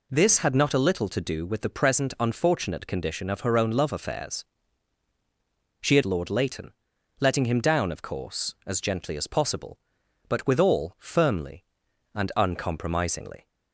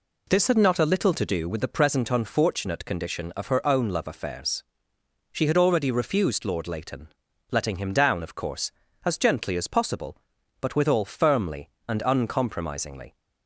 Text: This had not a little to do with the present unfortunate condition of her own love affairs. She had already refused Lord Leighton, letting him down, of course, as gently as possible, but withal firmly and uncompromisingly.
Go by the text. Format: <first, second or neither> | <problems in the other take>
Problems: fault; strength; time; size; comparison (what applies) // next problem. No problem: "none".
second | skips "already refused"; at 6.0 s